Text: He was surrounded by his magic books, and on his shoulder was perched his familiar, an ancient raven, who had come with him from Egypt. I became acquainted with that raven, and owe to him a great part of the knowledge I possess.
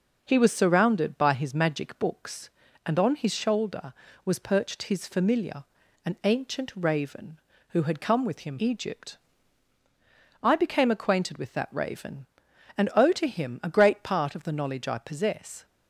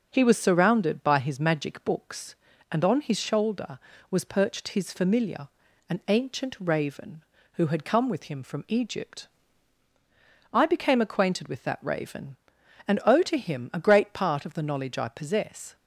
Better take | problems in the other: second | skips "from"; at 8.5 s

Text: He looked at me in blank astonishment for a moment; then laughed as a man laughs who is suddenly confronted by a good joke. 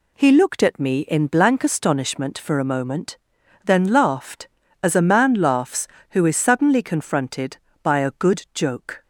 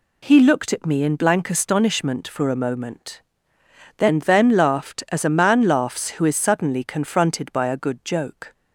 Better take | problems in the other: first | says "then" twice; at 4.1 s

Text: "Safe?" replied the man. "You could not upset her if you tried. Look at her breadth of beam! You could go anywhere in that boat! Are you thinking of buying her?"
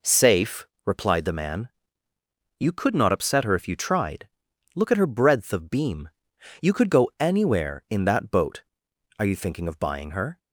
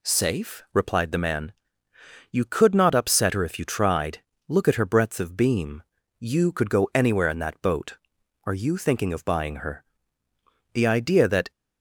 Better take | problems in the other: first | goes on to say "The idea that"; noticeable; from 10.7 s on; 0.78 s long

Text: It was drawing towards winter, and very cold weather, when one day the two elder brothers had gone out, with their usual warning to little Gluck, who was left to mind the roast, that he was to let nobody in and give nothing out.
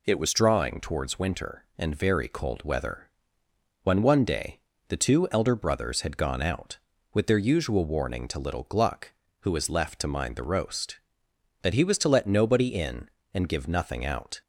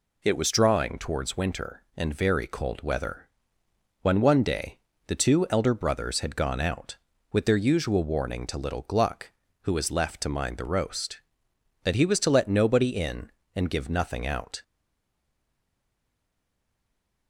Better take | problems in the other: first | pauses between "day" and "the"; slight; at 4.7 s; 0.28 s long; slight in the first // stays silent after the last word; strong; from 14.6 s on; 2.6 s long

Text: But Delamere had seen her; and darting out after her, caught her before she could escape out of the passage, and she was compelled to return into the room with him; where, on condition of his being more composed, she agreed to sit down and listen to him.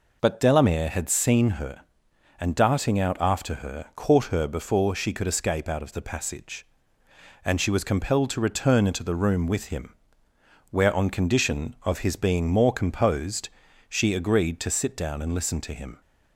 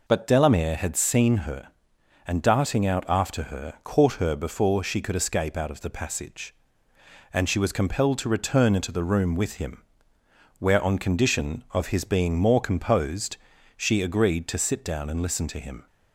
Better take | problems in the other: neither | none

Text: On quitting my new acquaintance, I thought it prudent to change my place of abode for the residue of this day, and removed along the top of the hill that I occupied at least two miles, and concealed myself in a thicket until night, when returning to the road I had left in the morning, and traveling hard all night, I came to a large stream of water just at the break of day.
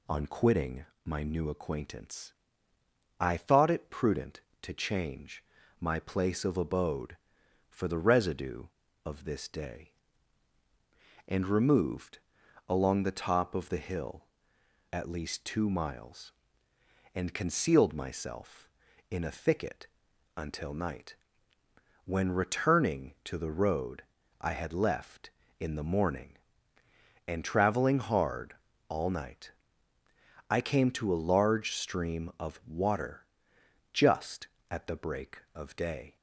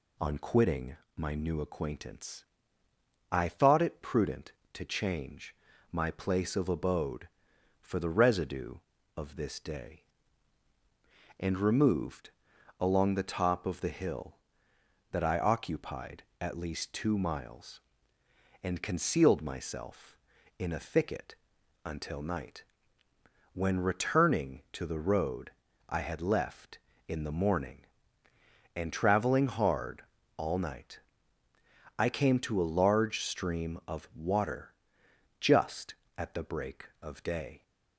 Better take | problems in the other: second | pauses between "quitting" and "my"; slight; at 0.8 s; 0.20 s long; slight in the second // pauses between "change" and "my"; at 5.4 s; 0.38 s long; also in the second // pauses between "removed" and "along"; noticeable; at 12.1 s; 0.48 s long; noticeable in the second // skips "that I occupied"; at 14.5 s // pauses between "thicket" and "until"; noticeable; at 19.8 s; 0.50 s long; noticeable in the second // pauses between "road" and "I"; slight; at 24.0 s; 0.36 s long; slight in the second // pauses between "hard" and "all"; slight; at 28.5 s; 0.34 s long; slight in the second // pauses between "water" and "just"; noticeable; at 33.2 s; 0.70 s long; noticeable in the second

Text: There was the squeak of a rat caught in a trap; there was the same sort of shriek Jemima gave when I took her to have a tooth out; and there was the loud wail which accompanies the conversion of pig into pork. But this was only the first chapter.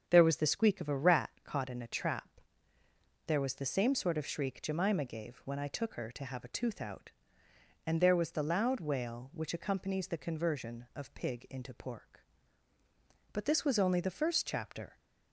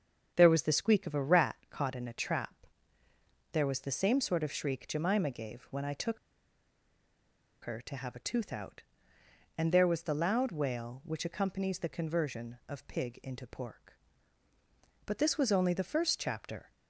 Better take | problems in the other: first | starts louder than the rest; strong; until 1.3 s; 7.5 dB; strong in the first // pauses between "took" and "her"; strong; at 6.1 s; 1.4 s long

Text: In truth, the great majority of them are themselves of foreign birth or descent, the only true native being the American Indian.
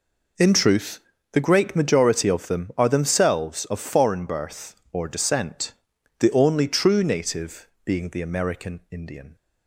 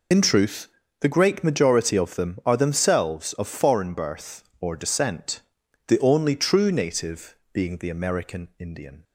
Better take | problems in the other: first | loses the start of "In"; at 0.1 s; 55 ms // pauses between "native" and "being"; slight; at 7.3 s; 0.18 s long; slight in the first

